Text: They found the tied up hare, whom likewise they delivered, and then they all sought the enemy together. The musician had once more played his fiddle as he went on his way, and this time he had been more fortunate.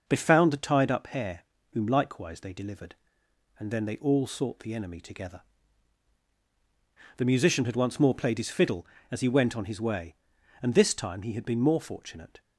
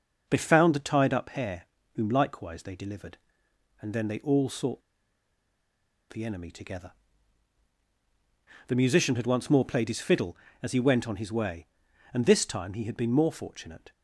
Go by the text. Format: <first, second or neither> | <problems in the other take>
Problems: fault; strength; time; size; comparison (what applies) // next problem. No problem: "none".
first | starts louder than the rest; noticeable; until 1.3 s; 6 dB // pauses between "sought" and "the"; strong; at 4.8 s; 1.2 s long